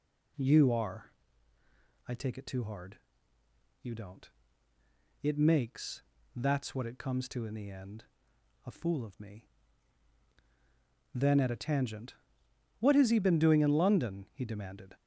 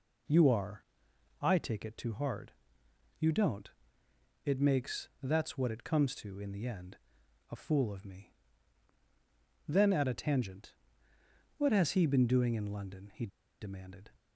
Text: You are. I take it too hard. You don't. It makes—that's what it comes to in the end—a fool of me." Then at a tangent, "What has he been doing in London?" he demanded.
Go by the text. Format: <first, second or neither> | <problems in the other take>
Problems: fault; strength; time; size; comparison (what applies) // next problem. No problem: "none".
first | pauses between "he" and "demanded"; slight; at 13.2 s; 0.33 s long